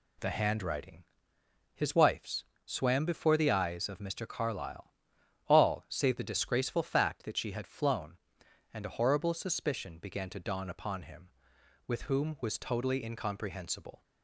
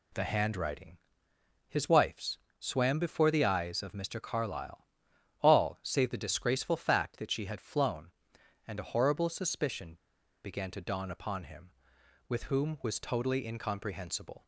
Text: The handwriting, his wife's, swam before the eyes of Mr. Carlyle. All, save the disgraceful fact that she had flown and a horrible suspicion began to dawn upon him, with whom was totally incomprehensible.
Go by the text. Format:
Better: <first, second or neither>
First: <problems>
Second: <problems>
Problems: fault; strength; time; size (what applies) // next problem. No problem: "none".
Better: first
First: none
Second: pauses between "suspicion" and "began"; noticeable; at 9.9 s; 0.48 s long